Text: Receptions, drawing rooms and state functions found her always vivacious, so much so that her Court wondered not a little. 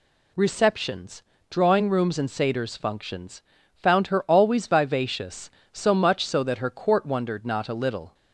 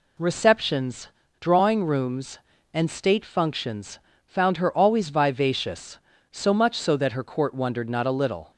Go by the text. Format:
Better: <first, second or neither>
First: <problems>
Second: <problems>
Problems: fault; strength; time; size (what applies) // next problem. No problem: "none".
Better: second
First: says "satyrs" for "state"; at 2.2 s // pauses between "functions" and "found"; slight; at 3.4 s; 0.32 s long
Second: pauses between "functions" and "found"; slight; at 3.9 s; 0.28 s long